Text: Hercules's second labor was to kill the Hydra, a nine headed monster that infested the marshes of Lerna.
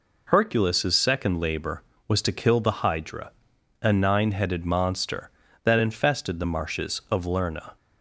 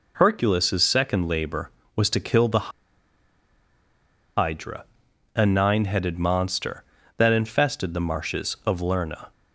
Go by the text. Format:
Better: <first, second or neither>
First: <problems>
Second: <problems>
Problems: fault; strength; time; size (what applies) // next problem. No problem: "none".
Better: first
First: none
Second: pauses between "the" and "Hydra"; strong; at 2.7 s; 1.6 s long